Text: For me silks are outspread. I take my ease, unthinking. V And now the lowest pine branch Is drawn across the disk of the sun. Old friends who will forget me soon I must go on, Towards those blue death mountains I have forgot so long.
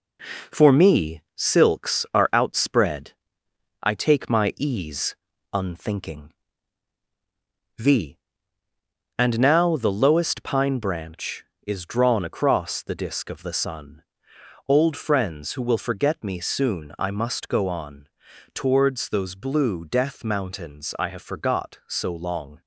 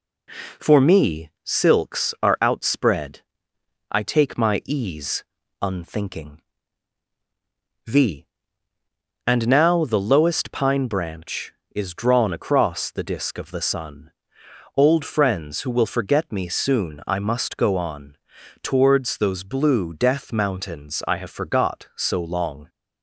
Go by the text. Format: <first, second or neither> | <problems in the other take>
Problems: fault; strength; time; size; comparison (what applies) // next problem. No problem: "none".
second | gets quieter; noticeable; throughout; 5 dB